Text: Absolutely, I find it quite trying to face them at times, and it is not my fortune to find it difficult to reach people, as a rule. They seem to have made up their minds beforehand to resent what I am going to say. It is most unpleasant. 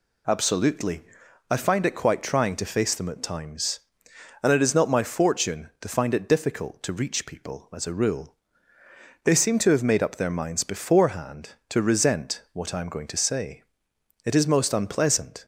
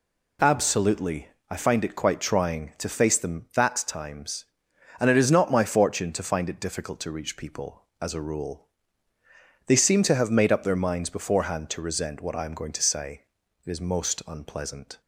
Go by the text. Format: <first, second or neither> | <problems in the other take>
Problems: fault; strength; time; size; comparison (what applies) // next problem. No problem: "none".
first | says "that" for "at"; at 3.5 s